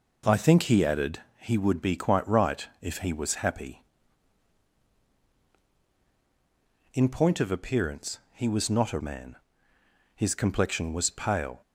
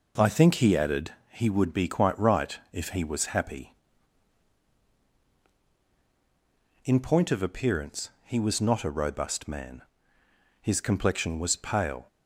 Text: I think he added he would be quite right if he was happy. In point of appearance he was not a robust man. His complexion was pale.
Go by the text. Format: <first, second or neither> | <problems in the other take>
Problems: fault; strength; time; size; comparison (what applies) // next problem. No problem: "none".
second | pauses between "added" and "he"; slight; at 1.2 s; 0.16 s long; slight in the second // skips "robust"; at 8.9 s